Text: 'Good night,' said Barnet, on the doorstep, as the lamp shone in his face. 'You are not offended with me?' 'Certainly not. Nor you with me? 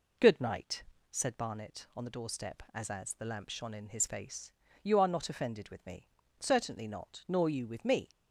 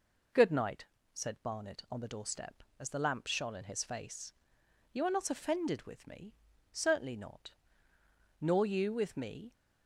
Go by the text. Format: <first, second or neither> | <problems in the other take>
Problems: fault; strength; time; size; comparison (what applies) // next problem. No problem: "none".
second | says "as" twice; at 2.8 s